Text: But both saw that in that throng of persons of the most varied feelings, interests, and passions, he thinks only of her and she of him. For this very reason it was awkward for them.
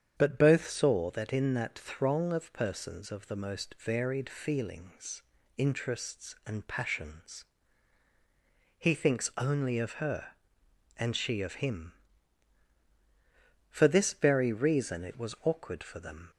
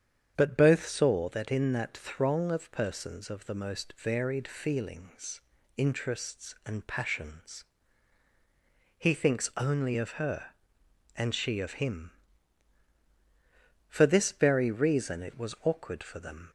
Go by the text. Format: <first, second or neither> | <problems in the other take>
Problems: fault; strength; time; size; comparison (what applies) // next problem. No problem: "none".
neither | starts louder than the rest; strong; the same in both